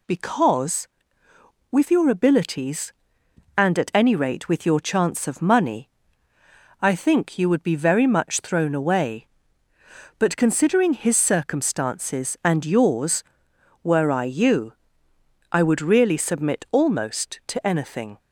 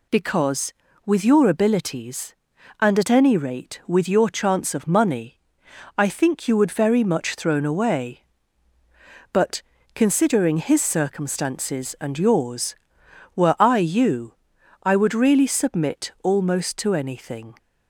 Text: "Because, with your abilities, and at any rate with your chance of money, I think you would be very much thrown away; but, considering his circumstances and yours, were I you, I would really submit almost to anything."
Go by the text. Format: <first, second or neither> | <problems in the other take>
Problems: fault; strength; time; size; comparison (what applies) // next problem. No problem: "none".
first | skips "be"; at 6.7 s